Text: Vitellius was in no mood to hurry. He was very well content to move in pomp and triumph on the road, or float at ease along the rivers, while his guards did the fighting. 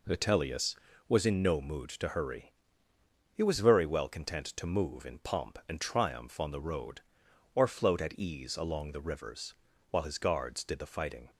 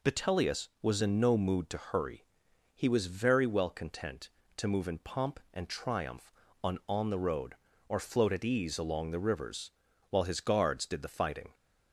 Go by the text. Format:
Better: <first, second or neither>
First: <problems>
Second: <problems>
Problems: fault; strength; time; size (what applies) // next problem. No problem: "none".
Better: first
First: none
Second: says "on" twice; at 6.8 s